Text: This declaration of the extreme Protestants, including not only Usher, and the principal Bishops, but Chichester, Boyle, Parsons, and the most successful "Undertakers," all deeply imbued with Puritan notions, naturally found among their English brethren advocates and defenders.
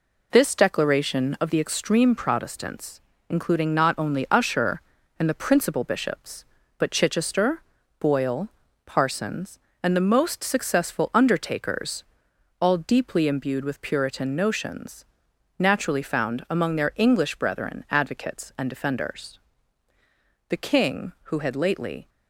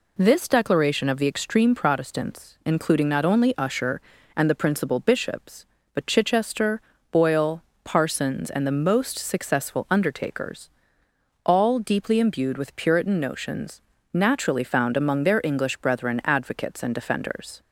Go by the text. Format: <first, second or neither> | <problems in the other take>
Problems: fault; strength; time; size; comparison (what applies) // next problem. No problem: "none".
second | goes on to say "The King who had lately"; from 20.4 s on; 1.6 s long